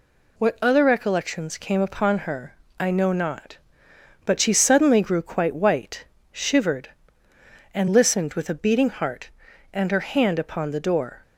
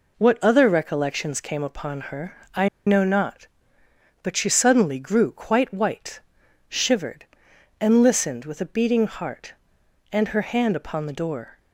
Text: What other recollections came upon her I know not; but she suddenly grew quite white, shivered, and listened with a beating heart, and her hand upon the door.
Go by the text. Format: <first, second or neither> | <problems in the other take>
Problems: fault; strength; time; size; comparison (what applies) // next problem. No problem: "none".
first | pauses between "her" and "I"; slight; at 2.3 s; 0.18 s long; slight in the first // pauses between "I" and "know"; slight; at 2.6 s; 0.18 s long